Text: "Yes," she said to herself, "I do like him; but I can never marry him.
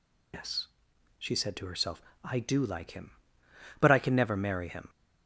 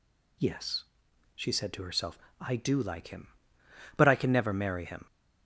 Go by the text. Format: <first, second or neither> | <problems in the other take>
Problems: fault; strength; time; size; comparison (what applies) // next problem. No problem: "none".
second | loses the start of "Yes"; at 0.3 s; 105 ms